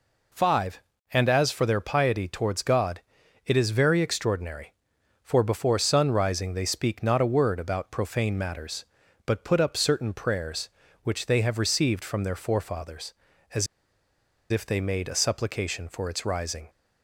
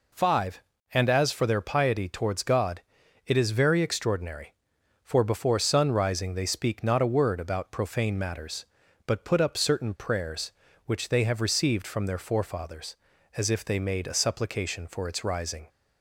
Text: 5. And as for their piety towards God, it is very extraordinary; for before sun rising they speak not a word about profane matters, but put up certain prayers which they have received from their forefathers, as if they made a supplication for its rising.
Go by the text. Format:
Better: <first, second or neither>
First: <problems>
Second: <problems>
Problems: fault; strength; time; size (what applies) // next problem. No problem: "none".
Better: second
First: pauses between "as" and "if"; noticeable; at 13.6 s; 0.84 s long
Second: none